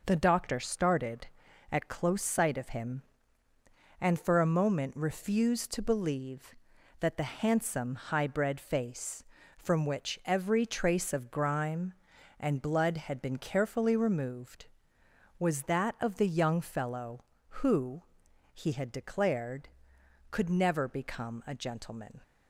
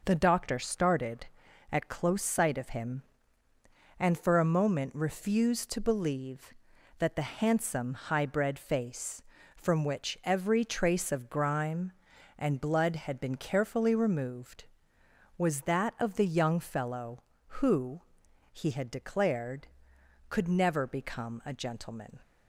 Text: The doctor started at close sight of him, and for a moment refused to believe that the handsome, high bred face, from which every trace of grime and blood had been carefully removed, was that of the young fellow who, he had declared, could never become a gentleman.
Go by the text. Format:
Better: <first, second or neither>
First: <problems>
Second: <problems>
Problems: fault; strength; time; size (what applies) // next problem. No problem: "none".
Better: neither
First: none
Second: none